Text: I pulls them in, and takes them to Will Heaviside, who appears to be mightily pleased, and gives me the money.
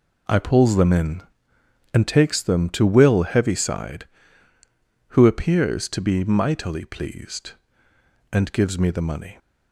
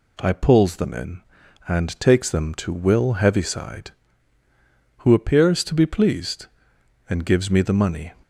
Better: first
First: none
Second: skips "mightily"; at 5.8 s

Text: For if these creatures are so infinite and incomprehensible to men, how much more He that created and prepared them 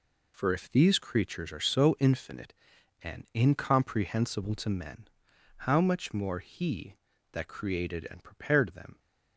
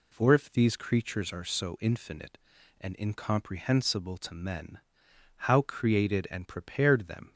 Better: first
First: none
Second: skips "much more He that"; at 5.6 s

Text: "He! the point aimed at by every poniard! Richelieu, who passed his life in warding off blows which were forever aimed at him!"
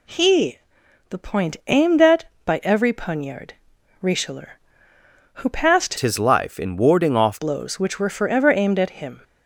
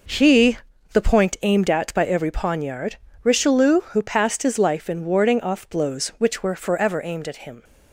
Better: second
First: changes voice from "his" to "off"; from 5.9 to 7.4 s; 1.5 s long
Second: none

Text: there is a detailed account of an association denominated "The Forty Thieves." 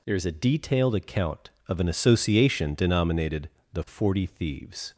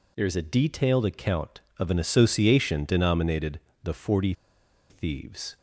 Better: first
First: pauses between "denominated" and "The"; slight; at 3.4 s; 0.24 s long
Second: pauses between "denominated" and "The"; slight; at 3.5 s; 0.24 s long // pauses between "Forty" and "Thieves"; noticeable; at 4.3 s; 0.57 s long

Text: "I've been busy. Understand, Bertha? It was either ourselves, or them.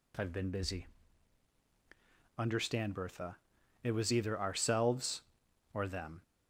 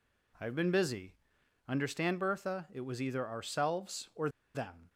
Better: first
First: none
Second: pauses between "or" and "them"; slight; at 4.2 s; 0.26 s long

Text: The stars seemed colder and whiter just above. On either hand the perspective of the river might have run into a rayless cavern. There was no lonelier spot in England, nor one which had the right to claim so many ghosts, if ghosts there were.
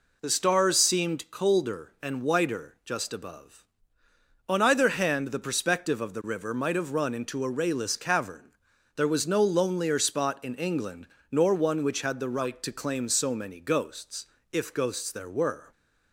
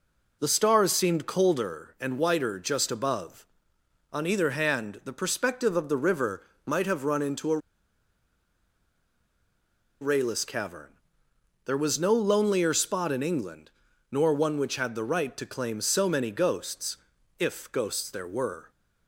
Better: first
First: none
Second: pauses between "river" and "might"; slight; at 6.4 s; 0.20 s long // pauses between "a" and "rayless"; strong; at 7.5 s; 2.4 s long

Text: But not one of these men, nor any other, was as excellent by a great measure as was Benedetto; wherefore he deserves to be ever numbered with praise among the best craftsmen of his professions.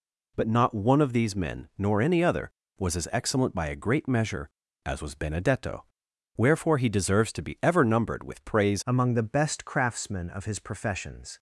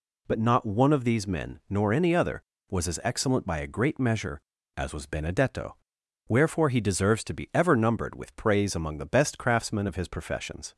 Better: second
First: changes voice at "among"; from 8.8 s on; 2.5 s long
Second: none

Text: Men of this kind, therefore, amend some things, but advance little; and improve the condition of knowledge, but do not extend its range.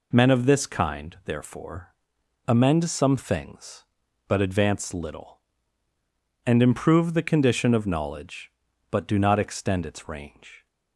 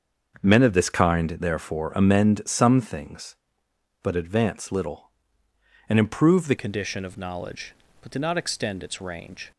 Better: first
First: none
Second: starts louder than the rest; until 1.4 s; 6.5 dB // changes voice at "condition"; from 6.5 s on; 3.0 s long

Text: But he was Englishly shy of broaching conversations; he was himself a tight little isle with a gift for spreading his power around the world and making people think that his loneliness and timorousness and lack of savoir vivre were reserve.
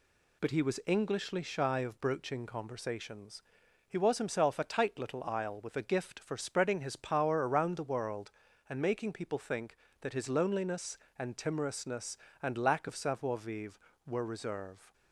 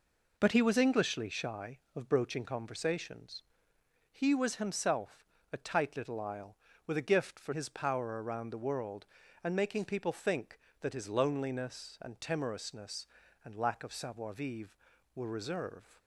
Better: first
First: none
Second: pauses between "himself" and "a"; slight; at 5.2 s; 0.26 s long // skips "spreading"; at 7.5 s

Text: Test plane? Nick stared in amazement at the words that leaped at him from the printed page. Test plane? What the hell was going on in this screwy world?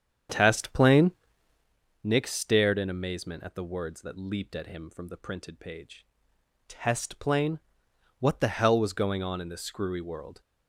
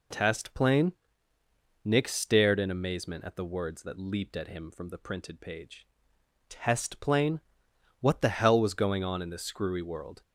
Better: second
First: starts louder than the rest; strong; until 1.7 s; 8.5 dB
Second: none

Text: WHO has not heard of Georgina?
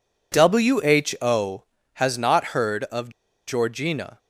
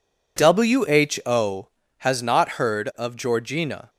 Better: second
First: pauses between "of" and "Georgina"; at 3.1 s; 0.36 s long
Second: none

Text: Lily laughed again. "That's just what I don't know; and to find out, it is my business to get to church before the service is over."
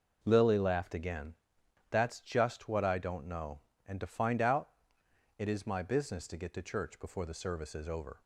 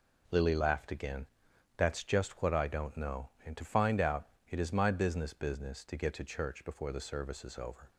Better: first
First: none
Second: says "business" twice; at 5.3 s

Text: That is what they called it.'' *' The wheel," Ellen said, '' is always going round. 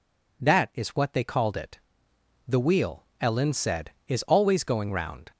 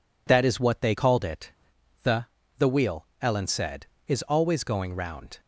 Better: first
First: none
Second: says "The" twice; at 2.5 s

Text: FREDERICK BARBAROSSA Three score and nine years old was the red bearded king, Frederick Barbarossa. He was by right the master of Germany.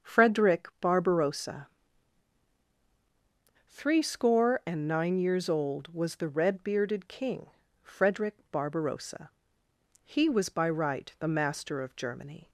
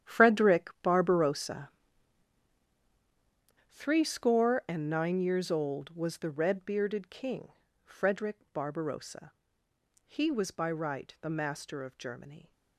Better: first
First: starts louder than the rest; until 1.1 s; 6.5 dB // pauses between "BARBAROSSA" and "Three"; strong; at 1.6 s; 2.0 s long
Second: gets quieter; strong; throughout; 15 dB // starts louder than the rest; strong; until 1.1 s; 10 dB // pauses between "BARBAROSSA" and "Three"; strong; at 1.6 s; 2.0 s long

